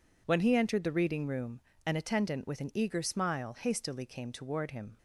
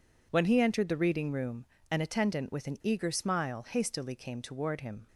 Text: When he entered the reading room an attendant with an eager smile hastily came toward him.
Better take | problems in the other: neither | pauses between "room" and "an"; slight; the same in both

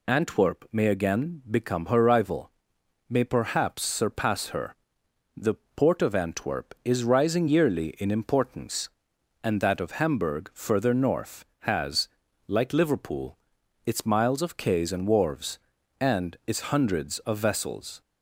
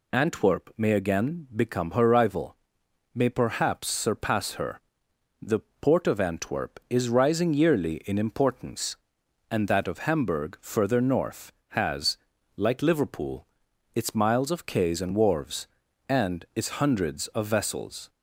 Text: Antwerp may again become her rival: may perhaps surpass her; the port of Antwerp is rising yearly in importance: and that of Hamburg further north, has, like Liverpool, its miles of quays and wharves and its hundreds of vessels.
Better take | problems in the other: neither | pauses between "the" and "port"; slight; the same in both

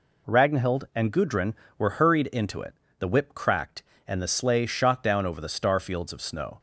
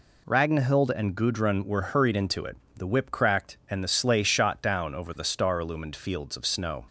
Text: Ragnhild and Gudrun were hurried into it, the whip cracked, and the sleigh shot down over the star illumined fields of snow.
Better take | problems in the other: second | skips "illumined"; at 5.7 s

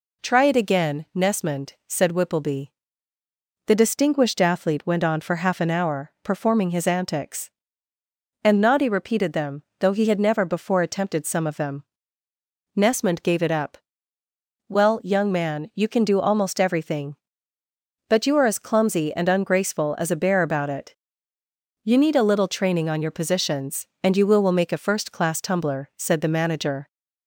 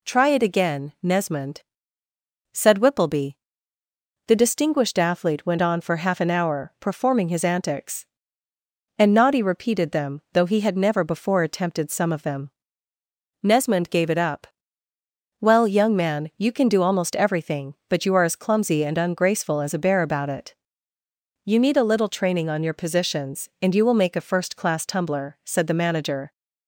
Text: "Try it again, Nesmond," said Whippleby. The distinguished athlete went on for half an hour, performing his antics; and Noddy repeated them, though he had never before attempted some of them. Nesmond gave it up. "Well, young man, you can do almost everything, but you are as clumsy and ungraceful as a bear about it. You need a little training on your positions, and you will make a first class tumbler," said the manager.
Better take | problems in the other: second | says "will" twice; at 24.4 s

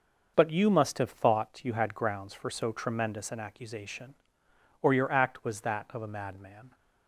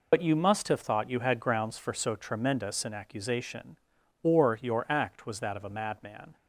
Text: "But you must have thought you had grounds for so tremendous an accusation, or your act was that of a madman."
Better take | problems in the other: first | loses the start of "But"; at 0.1 s; 70 ms

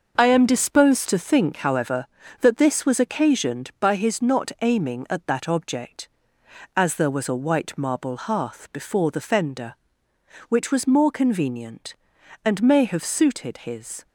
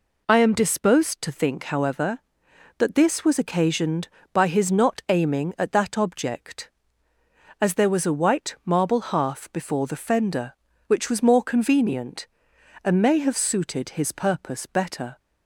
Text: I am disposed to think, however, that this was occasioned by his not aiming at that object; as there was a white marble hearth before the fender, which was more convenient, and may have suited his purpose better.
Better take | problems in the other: second | stops before "purpose better"; at 14.0 s

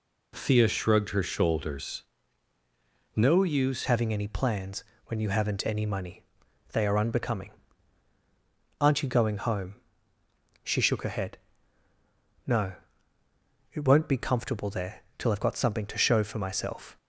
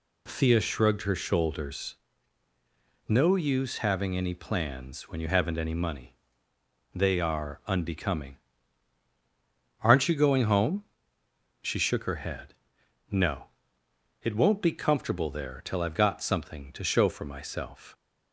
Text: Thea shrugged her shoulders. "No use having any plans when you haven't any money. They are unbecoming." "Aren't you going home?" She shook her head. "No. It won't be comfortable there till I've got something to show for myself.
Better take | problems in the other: second | changes voice at "having"; from 3.8 s on; 13.1 s long // pauses between "plans" and "when"; slight; at 4.8 s; 0.24 s long

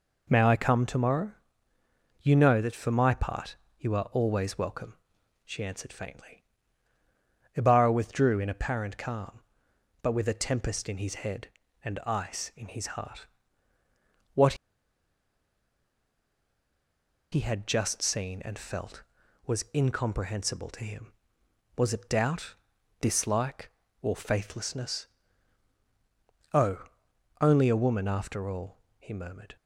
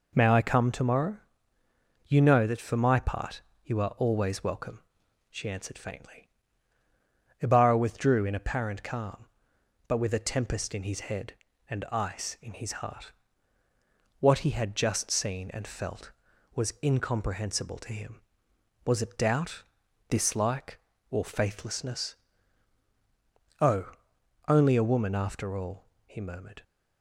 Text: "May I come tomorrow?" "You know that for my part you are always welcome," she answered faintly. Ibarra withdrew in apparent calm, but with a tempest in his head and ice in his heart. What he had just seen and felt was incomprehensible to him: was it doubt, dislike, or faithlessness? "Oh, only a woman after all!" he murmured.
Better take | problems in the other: second | pauses between "part" and "you"; slight; at 3.5 s; 0.22 s long; slight in the second // pauses between "What" and "he"; strong; at 14.5 s; 2.7 s long

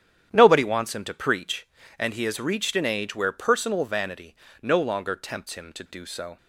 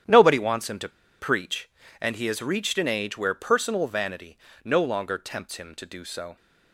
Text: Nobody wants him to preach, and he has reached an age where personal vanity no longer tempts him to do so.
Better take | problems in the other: first | starts louder than the rest; strong; until 1.3 s; 10 dB; strong in the first // pauses between "to" and "preach"; slight; at 0.8 s; 0.30 s long // pauses between "vanity" and "no"; slight; at 4.3 s; 0.26 s long; slight in the first

